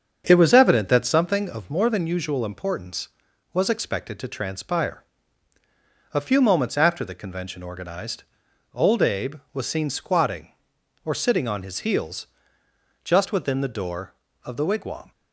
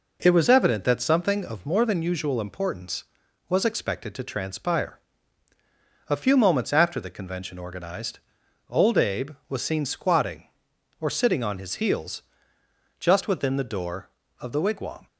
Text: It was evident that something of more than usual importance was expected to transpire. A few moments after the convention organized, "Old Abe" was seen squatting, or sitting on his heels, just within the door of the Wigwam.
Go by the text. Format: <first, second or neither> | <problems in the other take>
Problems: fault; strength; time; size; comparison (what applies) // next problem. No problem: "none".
second | starts louder than the rest; strong; until 1.3 s; 7 dB